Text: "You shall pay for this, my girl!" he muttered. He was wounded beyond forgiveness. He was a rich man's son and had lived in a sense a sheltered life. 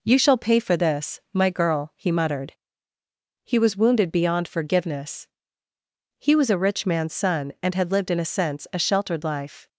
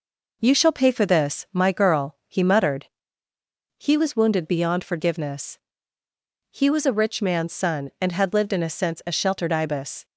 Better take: first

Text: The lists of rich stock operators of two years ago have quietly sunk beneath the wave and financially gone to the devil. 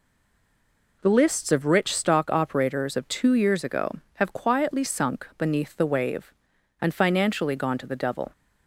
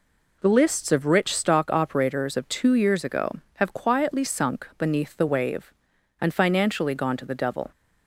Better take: second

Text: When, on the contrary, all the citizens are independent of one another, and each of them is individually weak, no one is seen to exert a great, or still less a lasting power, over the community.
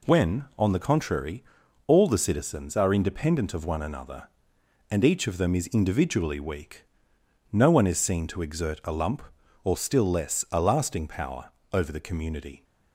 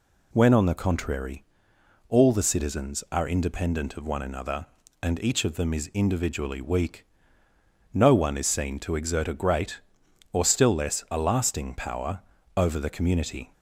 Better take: second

